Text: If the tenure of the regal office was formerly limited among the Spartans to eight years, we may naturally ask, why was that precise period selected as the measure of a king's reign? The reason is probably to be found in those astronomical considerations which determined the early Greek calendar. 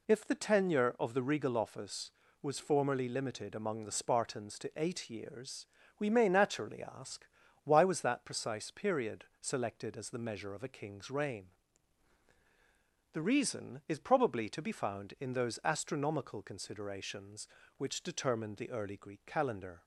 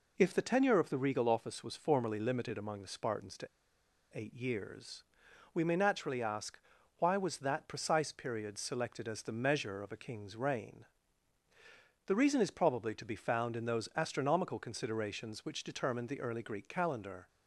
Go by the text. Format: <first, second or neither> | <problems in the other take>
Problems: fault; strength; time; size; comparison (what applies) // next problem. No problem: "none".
first | pauses between "to" and "eight"; noticeable; at 3.4 s; 0.67 s long